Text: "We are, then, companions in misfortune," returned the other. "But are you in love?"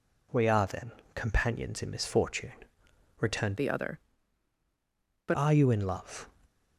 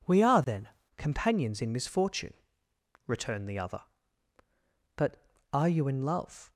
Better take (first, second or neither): second